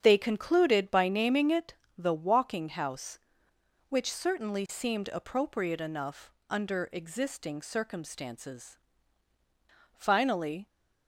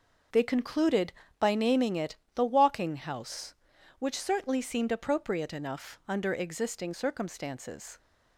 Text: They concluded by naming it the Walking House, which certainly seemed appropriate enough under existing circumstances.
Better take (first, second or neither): second